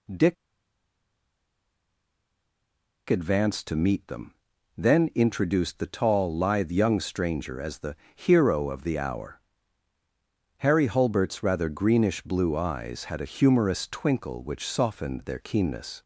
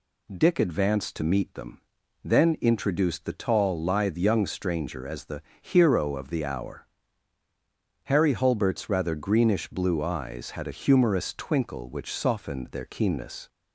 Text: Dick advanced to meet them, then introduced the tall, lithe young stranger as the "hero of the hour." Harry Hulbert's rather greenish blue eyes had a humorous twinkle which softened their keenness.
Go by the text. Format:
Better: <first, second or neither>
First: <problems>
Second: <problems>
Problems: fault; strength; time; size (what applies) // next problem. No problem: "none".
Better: second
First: pauses between "Dick" and "advanced"; strong; at 0.3 s; 2.7 s long // pauses between "the" and "hero"; slight; at 7.9 s; 0.18 s long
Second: pauses between "the" and "hero"; slight; at 5.4 s; 0.18 s long